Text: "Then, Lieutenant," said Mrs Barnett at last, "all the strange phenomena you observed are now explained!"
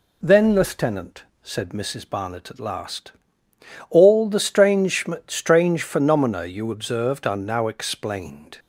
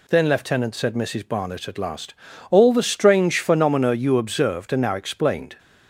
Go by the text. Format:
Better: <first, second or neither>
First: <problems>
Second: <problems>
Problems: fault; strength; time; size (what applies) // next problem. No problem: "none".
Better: second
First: says "strange" twice; at 5.2 s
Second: none